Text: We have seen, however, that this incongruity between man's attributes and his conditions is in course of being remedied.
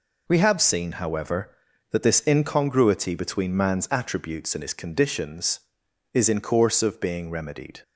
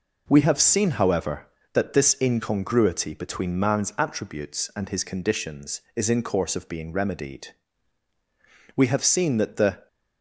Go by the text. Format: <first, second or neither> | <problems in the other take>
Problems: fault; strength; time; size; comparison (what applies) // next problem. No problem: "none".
first | goes on to say "We have seen that the"; noticeable; from 8.7 s on; 1.1 s long